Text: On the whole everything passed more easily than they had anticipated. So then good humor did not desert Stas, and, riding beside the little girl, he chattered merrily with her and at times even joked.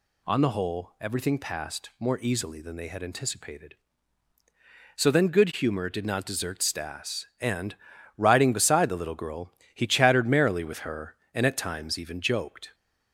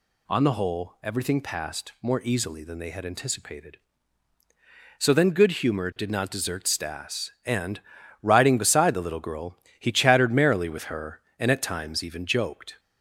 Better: neither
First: none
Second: none

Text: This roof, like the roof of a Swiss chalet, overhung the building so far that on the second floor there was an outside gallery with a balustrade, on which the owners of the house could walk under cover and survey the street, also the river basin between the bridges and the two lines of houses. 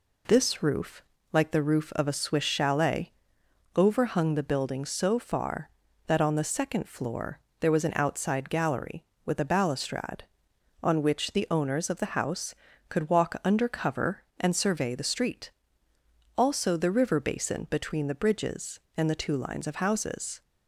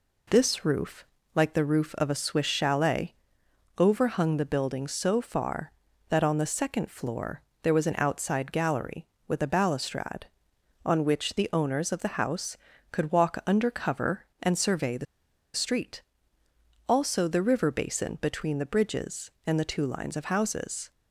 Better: first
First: pauses between "floor" and "there"; slight; at 7.3 s; 0.22 s long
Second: pauses between "floor" and "there"; slight; at 7.4 s; 0.22 s long // pauses between "the" and "street"; noticeable; at 15.0 s; 0.50 s long

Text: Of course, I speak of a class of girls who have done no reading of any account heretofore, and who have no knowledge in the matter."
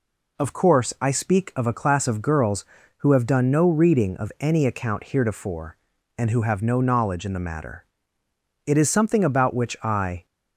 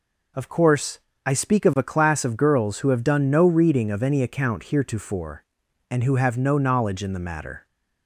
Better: second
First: goes on to say "It is something about which I"; from 8.6 s on; 1.6 s long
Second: none

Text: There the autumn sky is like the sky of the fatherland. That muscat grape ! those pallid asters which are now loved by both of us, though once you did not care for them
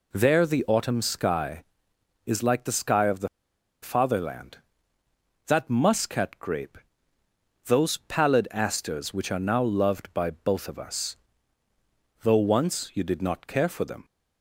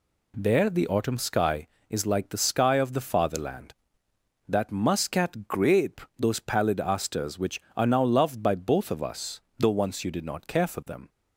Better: second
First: pauses between "the" and "fatherland"; noticeable; at 3.2 s; 0.54 s long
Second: none

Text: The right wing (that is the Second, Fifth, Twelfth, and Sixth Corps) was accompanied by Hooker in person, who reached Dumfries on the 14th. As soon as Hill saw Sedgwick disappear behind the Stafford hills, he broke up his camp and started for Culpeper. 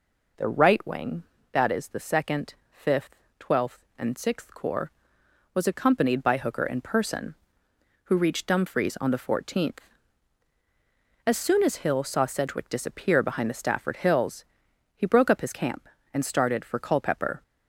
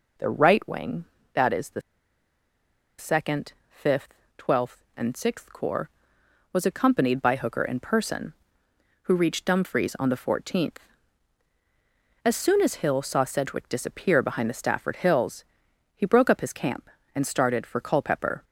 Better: first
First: none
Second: pauses between "the" and "Second"; at 1.8 s; 1.1 s long

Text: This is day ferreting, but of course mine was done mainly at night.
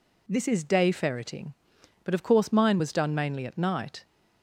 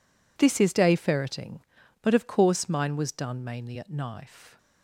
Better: first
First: none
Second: says "knife" for "night"; at 3.9 s

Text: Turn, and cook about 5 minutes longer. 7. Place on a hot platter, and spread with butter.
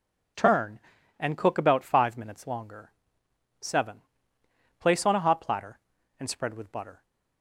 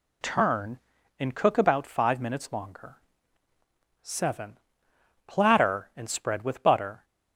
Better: first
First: none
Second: skips "Place on a hot"; at 4.9 s

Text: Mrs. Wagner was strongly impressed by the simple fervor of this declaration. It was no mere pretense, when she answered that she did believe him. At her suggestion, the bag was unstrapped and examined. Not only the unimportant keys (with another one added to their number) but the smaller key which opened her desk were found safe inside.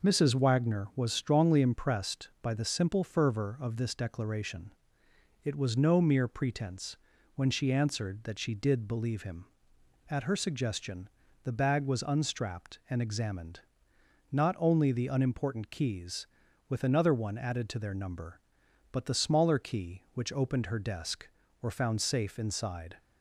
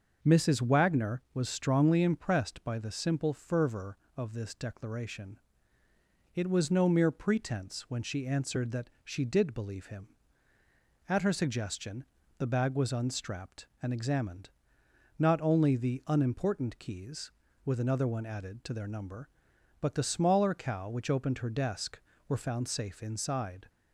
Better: first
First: none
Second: starts louder than the rest; until 1.2 s; 6 dB // says "cow" for "key"; at 20.5 s

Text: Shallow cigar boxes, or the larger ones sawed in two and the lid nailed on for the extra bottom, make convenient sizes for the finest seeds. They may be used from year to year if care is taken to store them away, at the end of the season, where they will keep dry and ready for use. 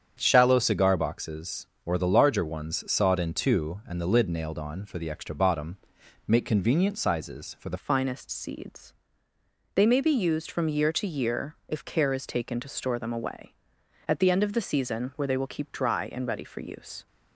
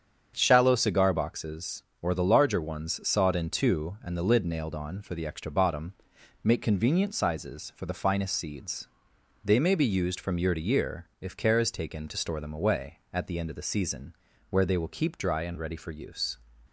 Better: second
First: starts louder than the rest; strong; until 1.2 s; 8 dB // changes voice at "finest"; from 7.7 s on; 9.3 s long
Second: starts louder than the rest; strong; until 1.3 s; 7.5 dB

